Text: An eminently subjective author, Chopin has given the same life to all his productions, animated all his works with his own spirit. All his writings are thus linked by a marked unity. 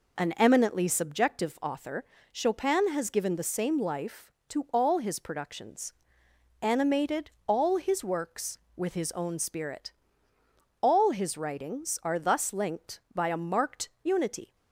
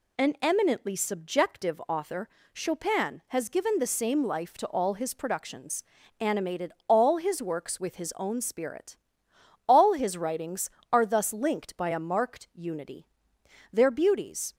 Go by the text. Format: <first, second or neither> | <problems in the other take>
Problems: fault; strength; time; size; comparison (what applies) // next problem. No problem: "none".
first | pauses between "animated" and "all"; slight; at 6.7 s; 0.16 s long; slight in the first // goes on to say "Their beauties"; noticeable; from 13.7 s on; 0.82 s long